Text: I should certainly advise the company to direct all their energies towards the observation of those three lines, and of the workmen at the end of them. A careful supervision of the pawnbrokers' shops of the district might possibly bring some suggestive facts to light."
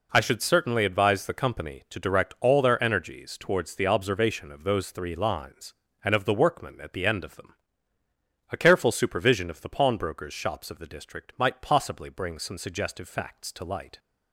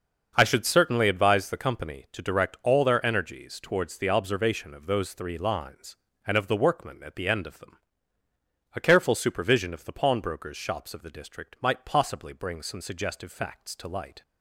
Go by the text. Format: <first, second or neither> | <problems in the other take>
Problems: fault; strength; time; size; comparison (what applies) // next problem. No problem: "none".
first | starts louder than the rest; until 1.5 s; 6.5 dB